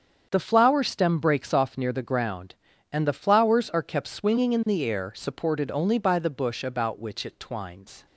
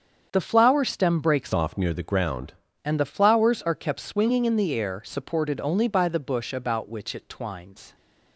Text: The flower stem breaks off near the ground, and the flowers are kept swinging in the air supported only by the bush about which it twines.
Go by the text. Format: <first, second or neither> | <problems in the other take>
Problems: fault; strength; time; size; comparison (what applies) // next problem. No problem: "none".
first | starts louder than the rest; strong; until 1.3 s; 7.5 dB; strong in the first // changes voice from "off" to "ground"; from 1.5 to 2.5 s; 1.0 s long